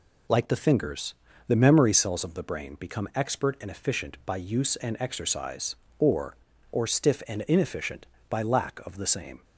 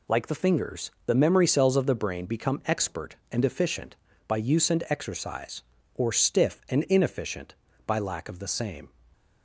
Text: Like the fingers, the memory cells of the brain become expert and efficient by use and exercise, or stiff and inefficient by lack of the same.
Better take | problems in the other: second | says "or" twice; at 6.7 s

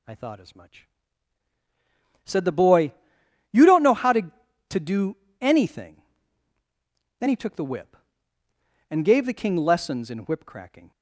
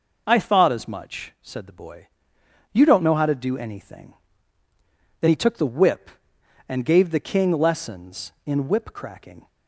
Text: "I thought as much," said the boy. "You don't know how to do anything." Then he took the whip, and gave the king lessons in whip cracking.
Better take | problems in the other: second | says "to" twice; at 4.7 s // pauses between "do" and "anything"; slight; at 5.1 s; 0.24 s long

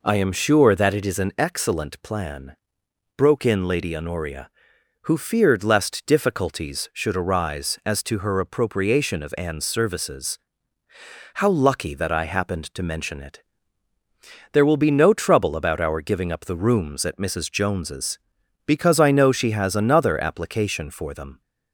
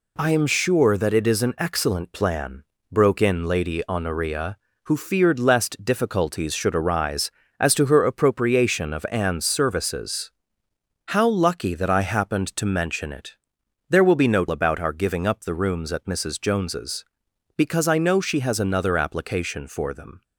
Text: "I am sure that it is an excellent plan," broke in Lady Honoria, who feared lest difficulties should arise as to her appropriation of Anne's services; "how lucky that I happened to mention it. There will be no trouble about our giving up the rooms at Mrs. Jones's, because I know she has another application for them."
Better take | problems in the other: first | skips "trouble"; at 14.4 s

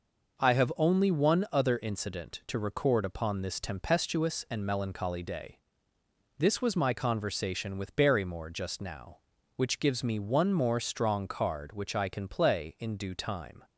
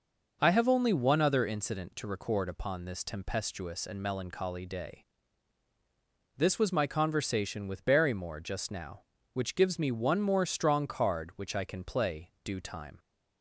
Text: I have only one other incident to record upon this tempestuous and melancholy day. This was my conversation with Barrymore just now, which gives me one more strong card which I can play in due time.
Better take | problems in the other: first | skips "in"; at 12.3 s

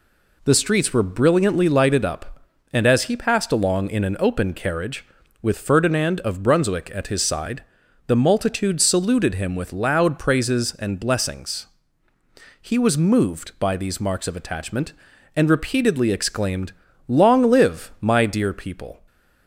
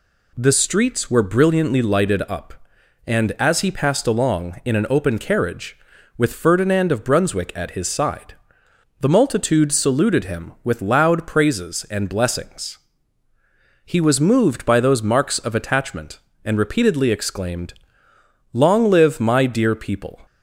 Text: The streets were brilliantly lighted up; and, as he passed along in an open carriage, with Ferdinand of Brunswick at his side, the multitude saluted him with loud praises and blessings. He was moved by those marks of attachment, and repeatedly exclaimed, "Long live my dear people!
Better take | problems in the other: second | says "these" for "those"; at 13.7 s

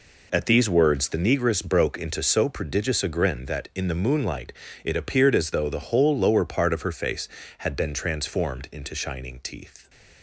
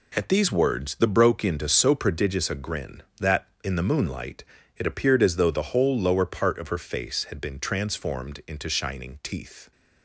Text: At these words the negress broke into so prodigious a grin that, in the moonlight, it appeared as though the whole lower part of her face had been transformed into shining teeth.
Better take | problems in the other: first | skips "negress"; at 1.0 s

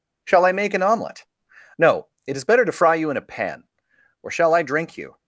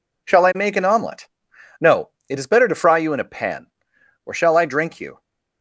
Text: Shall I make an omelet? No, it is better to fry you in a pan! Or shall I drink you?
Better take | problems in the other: neither | none

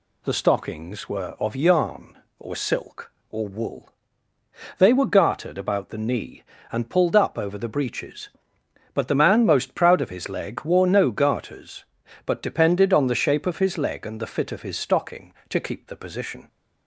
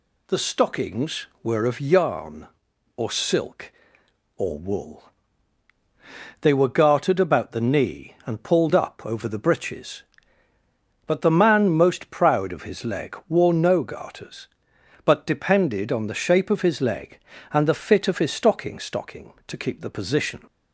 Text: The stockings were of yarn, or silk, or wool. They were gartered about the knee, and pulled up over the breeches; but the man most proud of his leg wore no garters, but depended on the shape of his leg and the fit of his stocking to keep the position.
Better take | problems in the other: first | says "stocking" twice; at 18.7 s

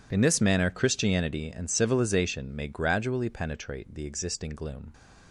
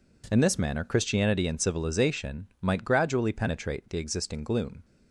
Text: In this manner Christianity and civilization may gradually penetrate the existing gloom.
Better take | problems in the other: first | says "might" for "may"; at 2.6 s

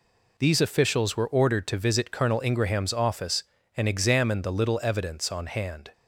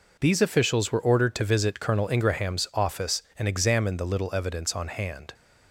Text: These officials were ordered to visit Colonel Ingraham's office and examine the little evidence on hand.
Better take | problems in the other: neither | none

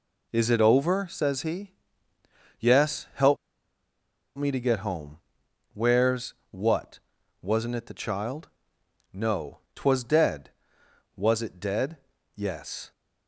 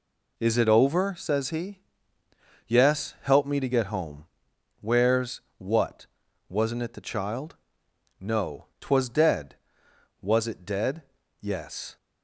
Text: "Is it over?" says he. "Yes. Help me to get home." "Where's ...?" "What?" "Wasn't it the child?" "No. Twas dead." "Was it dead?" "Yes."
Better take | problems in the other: second | pauses between "Help" and "me"; at 3.3 s; 1.0 s long

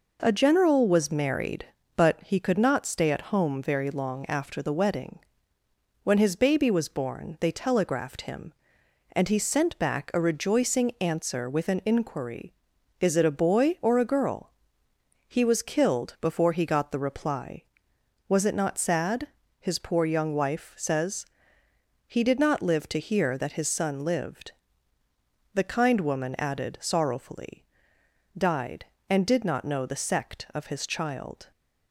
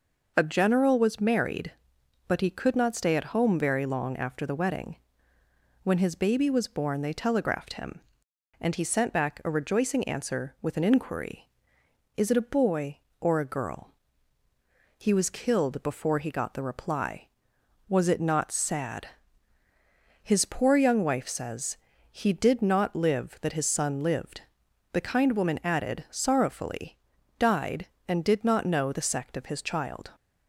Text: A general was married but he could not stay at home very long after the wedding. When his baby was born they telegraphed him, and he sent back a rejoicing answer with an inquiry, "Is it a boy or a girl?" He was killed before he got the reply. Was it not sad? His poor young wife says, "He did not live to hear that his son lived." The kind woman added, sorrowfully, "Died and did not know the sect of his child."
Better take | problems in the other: first | skips "to hear"; at 23.4 s

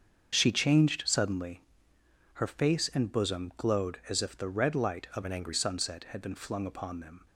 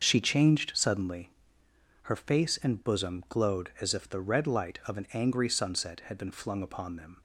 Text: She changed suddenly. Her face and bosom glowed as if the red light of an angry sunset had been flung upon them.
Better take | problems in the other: second | starts louder than the rest; strong; until 1.3 s; 7 dB; also in the second // changes voice from "an" to "angry"; from 5.2 to 5.5 s; 0.3 s long

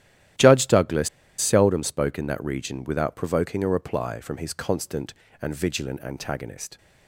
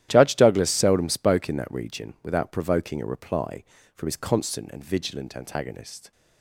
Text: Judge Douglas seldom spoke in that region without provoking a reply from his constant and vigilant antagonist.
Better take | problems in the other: second | starts louder than the rest; strong; until 1.6 s; 12 dB; strong in the second // pauses between "Douglas" and "seldom"; slight; at 1.0 s; 0.30 s long

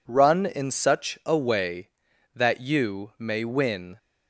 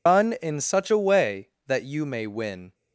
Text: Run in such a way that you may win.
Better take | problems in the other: first | loses the start of "Run"; at 0.0 s; 135 ms

